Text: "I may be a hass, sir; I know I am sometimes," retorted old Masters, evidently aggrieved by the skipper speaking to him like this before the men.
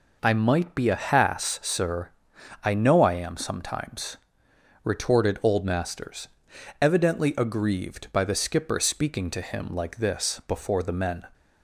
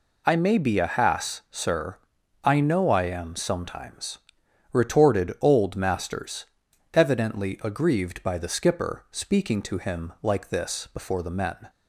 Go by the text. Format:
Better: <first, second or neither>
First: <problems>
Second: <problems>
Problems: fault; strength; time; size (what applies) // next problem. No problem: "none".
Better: second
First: says "might" for "may"; at 0.3 s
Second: none